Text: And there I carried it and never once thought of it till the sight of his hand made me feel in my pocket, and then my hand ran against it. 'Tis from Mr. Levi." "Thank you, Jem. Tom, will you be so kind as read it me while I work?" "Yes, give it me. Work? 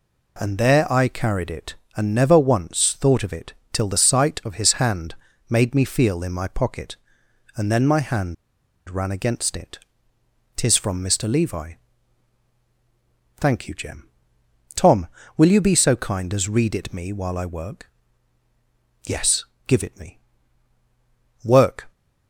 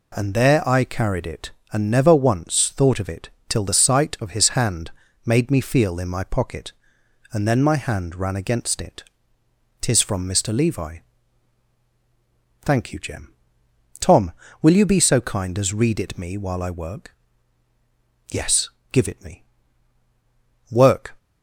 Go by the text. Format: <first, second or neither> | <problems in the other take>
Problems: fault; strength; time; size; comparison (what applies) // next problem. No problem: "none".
second | pauses between "it" and "till"; slight; at 3.5 s; 0.20 s long; slight in the second // pauses between "hand" and "made"; slight; at 5.1 s; 0.34 s long; slight in the second // pauses between "hand" and "ran"; noticeable; at 8.3 s; 0.53 s long